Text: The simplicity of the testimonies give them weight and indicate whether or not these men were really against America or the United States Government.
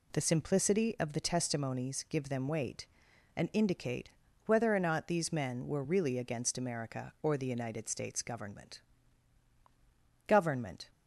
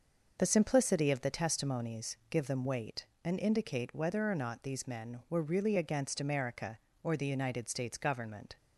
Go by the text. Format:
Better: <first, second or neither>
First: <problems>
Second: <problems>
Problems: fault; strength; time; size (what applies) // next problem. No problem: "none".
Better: second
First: pauses between "indicate" and "whether"; slight; at 4.1 s; 0.36 s long // says "Government" twice; at 10.2 s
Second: none